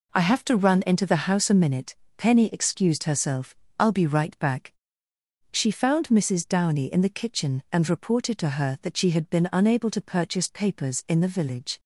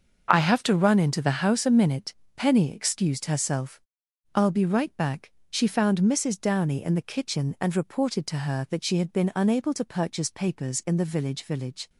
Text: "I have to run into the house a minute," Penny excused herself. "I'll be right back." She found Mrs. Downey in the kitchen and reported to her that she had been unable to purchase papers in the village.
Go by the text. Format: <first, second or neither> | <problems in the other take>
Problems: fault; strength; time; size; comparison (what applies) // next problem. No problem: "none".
first | starts louder than the rest; noticeable; until 1.3 s; 6 dB // says "village" twice; at 11.4 s